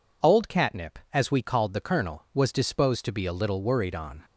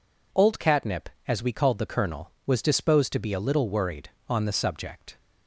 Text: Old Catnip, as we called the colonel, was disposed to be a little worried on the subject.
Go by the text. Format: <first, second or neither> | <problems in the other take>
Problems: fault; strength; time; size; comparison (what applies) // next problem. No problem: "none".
second | stops before "the subject"; at 4.2 s